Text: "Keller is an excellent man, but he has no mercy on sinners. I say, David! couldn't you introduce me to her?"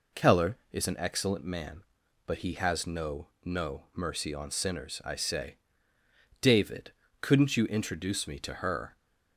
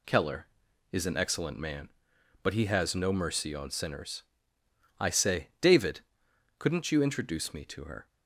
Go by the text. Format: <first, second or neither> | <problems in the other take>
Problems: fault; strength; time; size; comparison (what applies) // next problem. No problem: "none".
second | says "no" twice; at 3.4 s